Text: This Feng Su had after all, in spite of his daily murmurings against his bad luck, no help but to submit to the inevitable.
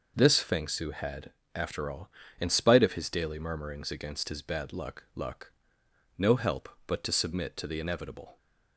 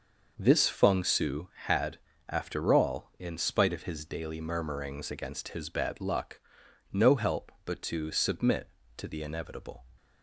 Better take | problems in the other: second | pauses between "had" and "after"; slight; at 1.3 s; 0.26 s long; slight in the second // says "luck" twice; at 5.1 s

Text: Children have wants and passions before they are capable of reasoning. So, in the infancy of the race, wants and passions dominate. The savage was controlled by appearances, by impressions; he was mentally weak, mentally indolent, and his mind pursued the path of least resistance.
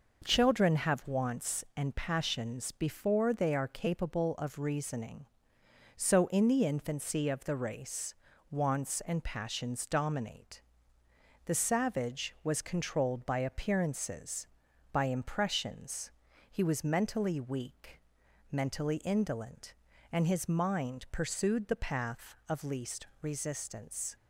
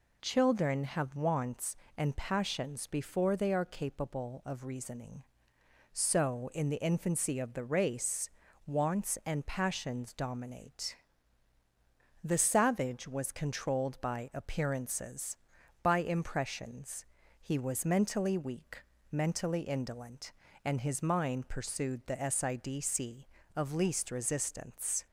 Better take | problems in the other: first | says "sidc" for "path"; at 22.1 s

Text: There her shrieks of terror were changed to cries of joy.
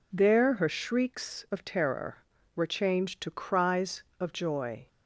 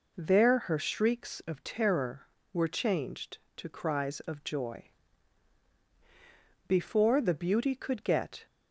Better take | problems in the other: first | goes on to say "Before The Beauty could get"; strong; from 6.6 s on; 1.7 s long

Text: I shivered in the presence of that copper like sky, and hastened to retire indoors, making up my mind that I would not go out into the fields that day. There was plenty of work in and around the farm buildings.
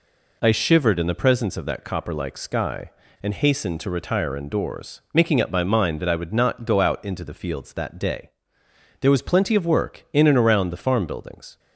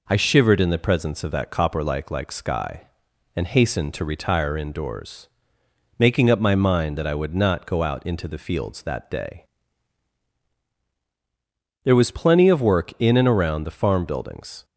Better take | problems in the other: first | says "like" twice; at 2.1 s

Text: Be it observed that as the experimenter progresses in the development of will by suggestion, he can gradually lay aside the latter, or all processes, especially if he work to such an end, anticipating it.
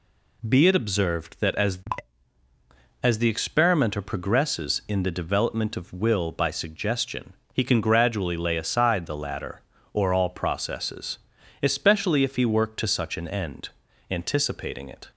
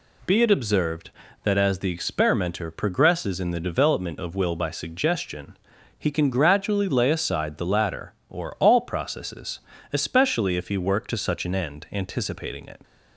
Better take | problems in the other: second | says "as" twice; at 3.0 s

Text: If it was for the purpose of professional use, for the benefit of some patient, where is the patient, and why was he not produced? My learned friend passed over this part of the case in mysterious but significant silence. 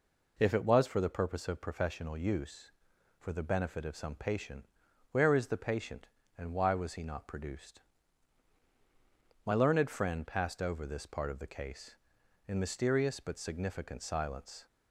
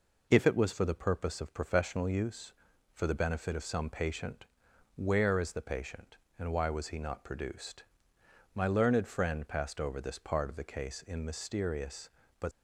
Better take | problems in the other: first | stops before "significant silence"; at 12.5 s

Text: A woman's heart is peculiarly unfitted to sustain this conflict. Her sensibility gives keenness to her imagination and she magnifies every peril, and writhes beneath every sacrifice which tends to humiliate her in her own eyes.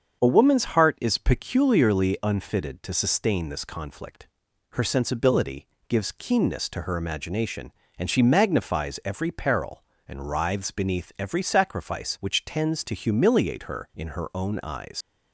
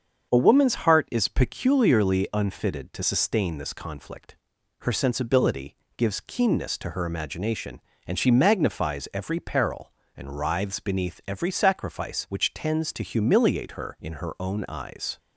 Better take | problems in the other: second | starts louder than the rest; until 1.2 s; 7 dB; also in the second // pauses between "sensibility" and "gives"; slight; at 5.6 s; 0.22 s long; slight in the second // leaves "eyes" unfinished; at 15.0 s; 115 ms

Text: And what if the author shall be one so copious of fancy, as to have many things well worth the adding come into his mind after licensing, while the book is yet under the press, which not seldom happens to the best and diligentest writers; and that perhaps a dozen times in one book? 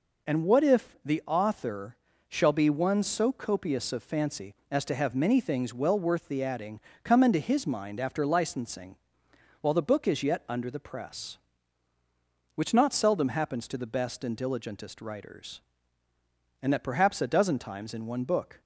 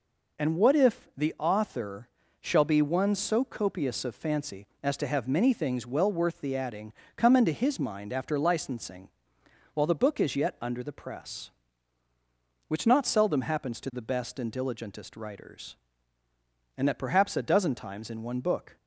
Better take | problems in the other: neither | pauses between "author" and "shall"; slight; the same in both // pauses between "adding" and "come"; slight; the same in both

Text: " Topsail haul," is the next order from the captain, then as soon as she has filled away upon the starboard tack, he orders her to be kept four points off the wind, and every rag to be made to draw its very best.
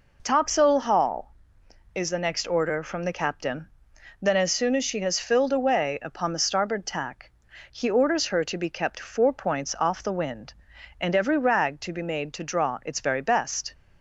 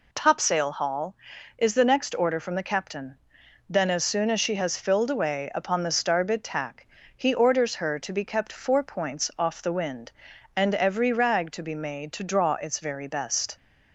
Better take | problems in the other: neither | none

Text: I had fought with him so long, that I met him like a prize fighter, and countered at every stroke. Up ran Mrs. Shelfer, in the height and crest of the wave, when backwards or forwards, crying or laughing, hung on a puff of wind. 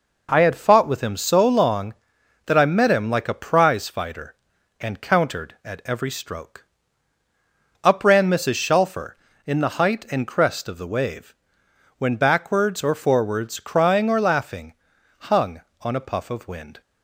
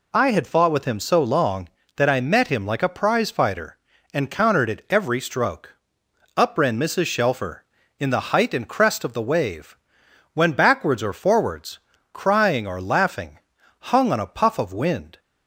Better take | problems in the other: neither | none

